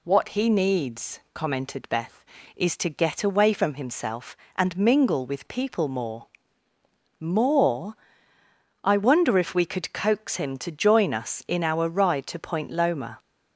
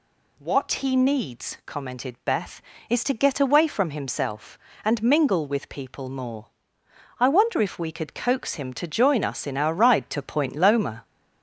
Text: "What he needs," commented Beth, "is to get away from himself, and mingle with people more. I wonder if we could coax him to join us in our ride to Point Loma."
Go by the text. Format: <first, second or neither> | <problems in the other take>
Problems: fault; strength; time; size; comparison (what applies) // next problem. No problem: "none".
second | says "more" twice; at 7.1 s